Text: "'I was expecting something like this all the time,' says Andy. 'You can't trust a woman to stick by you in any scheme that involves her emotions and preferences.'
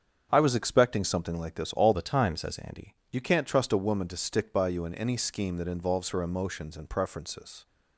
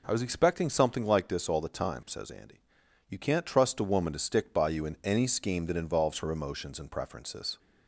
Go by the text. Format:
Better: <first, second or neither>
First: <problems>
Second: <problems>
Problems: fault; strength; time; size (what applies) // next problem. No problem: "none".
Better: second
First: starts louder than the rest; strong; until 1.3 s; 7 dB // changes voice from "the" to "Andy"; from 1.9 to 2.9 s; 1.0 s long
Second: none